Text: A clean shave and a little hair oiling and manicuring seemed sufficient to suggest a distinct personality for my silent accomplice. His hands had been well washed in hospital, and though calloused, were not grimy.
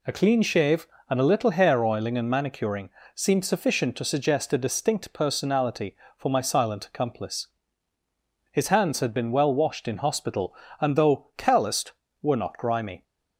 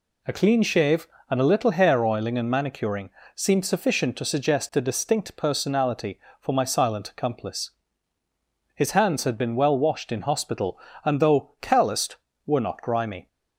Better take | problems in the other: neither | pauses between "manicuring" and "seemed"; slight; the same in both

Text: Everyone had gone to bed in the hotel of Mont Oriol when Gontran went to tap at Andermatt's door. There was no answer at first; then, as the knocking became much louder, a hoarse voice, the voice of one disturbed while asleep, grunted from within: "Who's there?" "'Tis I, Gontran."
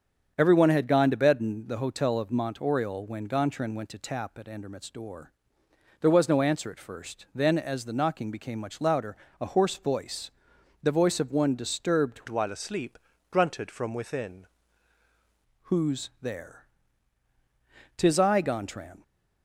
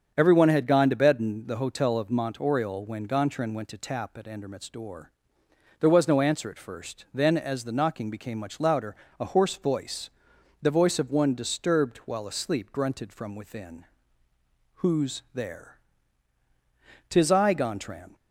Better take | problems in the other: second | starts louder than the rest; strong; until 1.3 s; 7.5 dB; strong in the second // changes voice from "while" to "within"; from 12.2 to 14.4 s; 2.2 s long

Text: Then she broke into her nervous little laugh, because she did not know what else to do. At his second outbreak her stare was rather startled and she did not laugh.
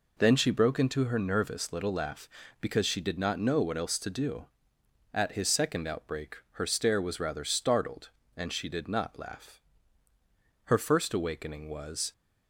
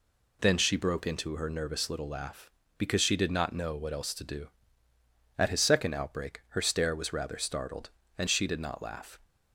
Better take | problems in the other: second | pauses between "outbreak" and "her"; slight; at 6.3 s; 0.16 s long // goes on to say "Her first awakening was"; from 10.6 s on; 1.4 s long

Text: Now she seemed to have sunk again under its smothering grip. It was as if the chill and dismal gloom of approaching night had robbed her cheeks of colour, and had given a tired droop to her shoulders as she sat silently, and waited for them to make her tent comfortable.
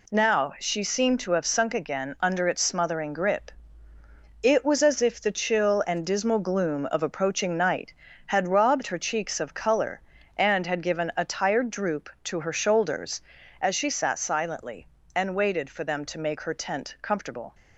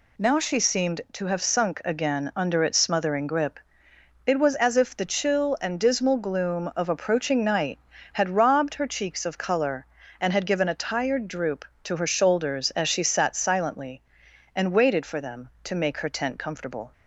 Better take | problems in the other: neither | none

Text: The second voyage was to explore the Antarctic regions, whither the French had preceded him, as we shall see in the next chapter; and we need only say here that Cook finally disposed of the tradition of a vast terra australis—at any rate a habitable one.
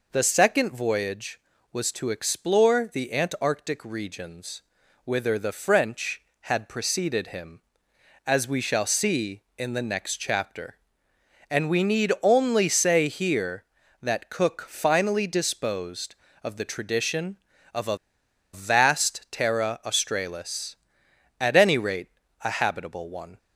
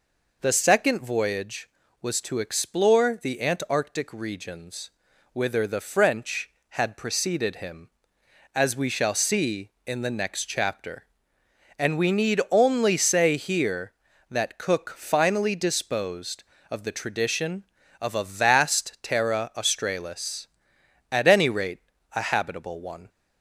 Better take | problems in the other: second | pauses between "a" and "vast"; noticeable; at 17.9 s; 0.55 s long // pauses between "rate" and "a"; slight; at 22.0 s; 0.32 s long; slight in the second

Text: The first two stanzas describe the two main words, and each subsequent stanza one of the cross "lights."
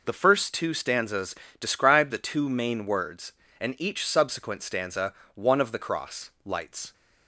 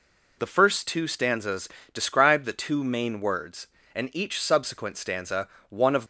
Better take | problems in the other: first | pauses between "stanzas" and "describe"; slight; at 1.6 s; 0.26 s long; slight in the first // pauses between "stanza" and "one"; slight; at 5.4 s; 0.22 s long; slight in the first // stops before "the cross lights"; at 6.0 s

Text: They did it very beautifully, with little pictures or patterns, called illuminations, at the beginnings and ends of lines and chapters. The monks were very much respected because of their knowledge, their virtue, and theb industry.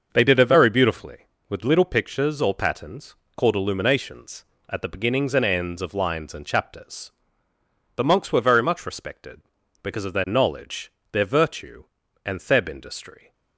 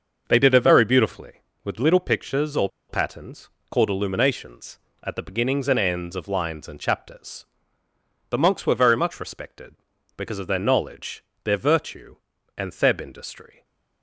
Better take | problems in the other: first | starts louder than the rest; until 1.2 s; 6.5 dB; also in the first // pauses between "or" and "patterns"; slight; at 2.6 s; 0.22 s long // stays silent after the last word; slight; from 13.5 s on; 0.5 s long

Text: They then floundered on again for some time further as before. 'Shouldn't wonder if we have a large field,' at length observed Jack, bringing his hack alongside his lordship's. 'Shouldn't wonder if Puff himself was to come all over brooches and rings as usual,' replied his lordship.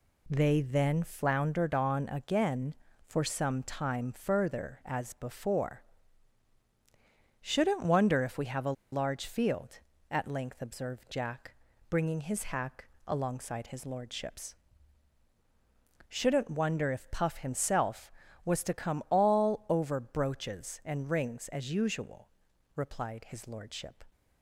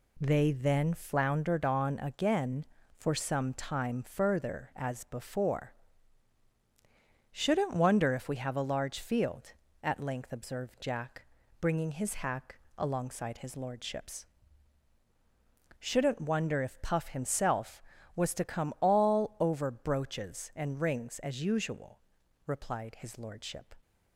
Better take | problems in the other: second | pauses between "a" and "large"; slight; at 8.7 s; 0.19 s long // pauses between "hack" and "alongside"; slight; at 12.8 s; 0.18 s long; slight in the second

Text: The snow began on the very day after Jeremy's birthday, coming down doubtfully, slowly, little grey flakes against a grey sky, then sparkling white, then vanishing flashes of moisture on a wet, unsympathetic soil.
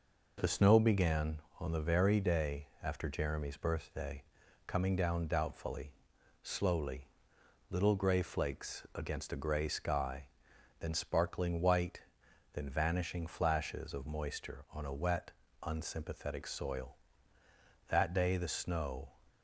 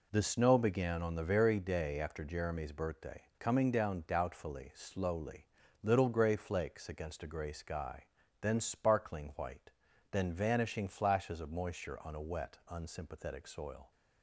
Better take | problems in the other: second | goes on to say "That day the snow"; noticeable; from 17.8 s on; 1.2 s long

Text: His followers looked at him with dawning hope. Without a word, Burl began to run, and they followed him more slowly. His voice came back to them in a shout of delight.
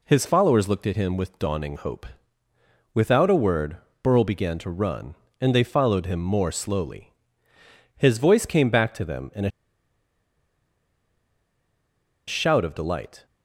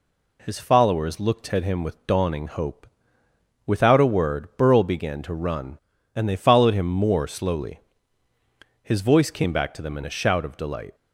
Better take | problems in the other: second | pauses between "a" and "shout"; strong; at 9.5 s; 2.7 s long

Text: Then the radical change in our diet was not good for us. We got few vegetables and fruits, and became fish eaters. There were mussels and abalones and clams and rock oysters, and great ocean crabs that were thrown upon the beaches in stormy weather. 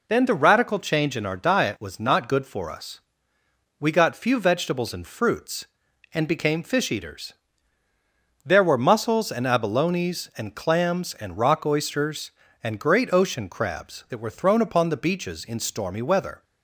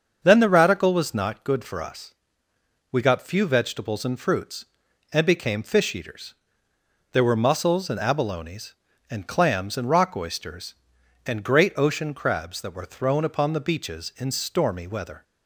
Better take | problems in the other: first | starts louder than the rest; until 1.2 s; 6.5 dB // skips "change in our diet"; at 0.9 s

